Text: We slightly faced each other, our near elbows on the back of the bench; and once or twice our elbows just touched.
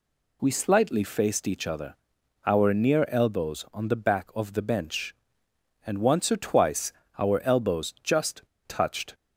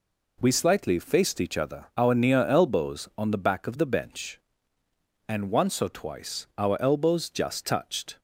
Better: second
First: pauses between "twice" and "our"; slight; at 6.9 s; 0.26 s long // pauses between "just" and "touched"; slight; at 8.4 s; 0.25 s long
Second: none

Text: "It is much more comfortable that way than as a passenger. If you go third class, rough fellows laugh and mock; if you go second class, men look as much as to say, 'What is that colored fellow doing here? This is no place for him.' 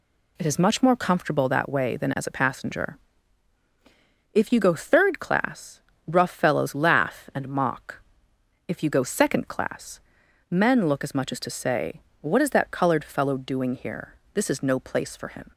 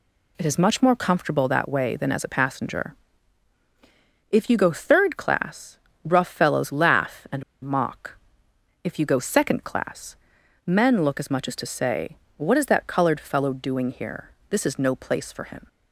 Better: first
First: none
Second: pauses between "and" and "mock"; slight; at 7.4 s; 0.20 s long

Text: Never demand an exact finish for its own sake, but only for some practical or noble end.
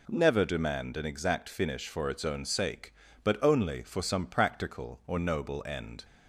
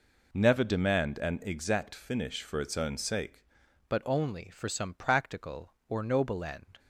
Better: first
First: none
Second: changes voice at "but"; from 3.8 s on; 2.9 s long

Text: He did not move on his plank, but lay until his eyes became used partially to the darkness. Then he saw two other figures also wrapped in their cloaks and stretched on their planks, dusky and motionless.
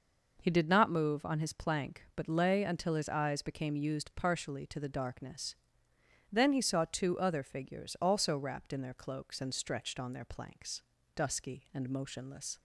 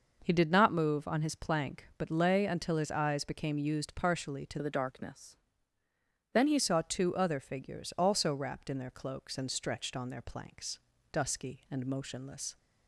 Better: first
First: none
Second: changes voice from "the" to "he"; from 4.6 to 6.5 s; 1.9 s long

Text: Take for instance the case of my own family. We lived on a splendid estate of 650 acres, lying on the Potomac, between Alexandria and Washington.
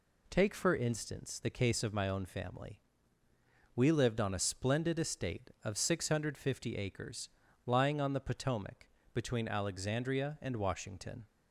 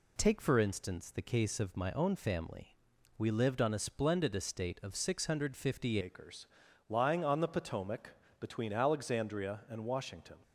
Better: first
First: none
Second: changes voice at "acres"; from 6.0 s on; 4.3 s long

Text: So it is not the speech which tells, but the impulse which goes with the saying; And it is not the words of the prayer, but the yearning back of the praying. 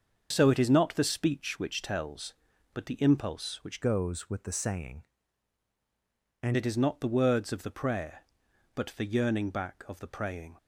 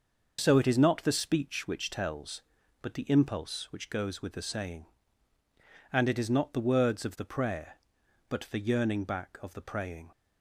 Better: second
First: starts louder than the rest; until 1.3 s; 6.5 dB // changes voice from "goes" to "And"; from 3.8 to 6.5 s; 2.7 s long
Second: starts louder than the rest; noticeable; until 1.4 s; 6 dB

